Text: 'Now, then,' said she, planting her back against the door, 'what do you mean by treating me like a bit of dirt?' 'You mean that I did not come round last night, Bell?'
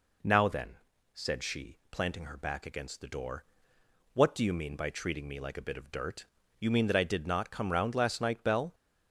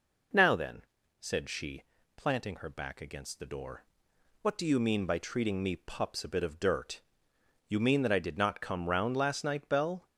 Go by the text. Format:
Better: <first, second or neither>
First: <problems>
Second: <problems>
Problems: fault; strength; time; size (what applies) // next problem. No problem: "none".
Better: first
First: none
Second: says "pups" for "like"; at 5.7 s